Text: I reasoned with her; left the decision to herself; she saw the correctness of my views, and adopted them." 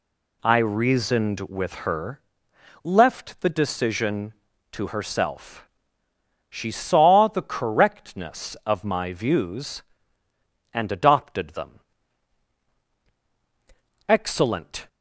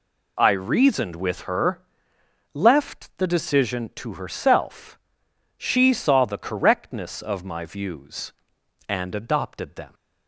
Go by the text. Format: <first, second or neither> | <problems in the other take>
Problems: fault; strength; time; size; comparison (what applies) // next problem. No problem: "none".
second | goes on to say "Excellent"; noticeable; from 14.0 s on; 0.80 s long